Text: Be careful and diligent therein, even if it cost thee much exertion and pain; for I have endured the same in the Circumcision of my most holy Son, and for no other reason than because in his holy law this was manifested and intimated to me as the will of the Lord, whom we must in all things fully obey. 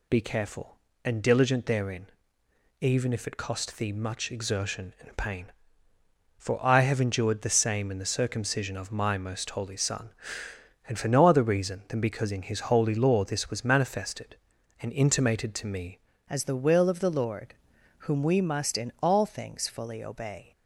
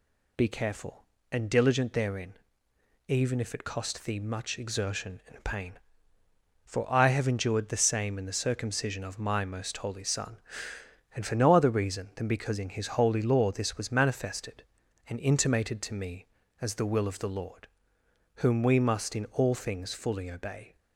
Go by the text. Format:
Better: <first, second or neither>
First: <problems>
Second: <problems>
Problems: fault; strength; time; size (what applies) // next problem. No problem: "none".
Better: second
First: changes voice at "as"; from 16.2 s on; 4.3 s long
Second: none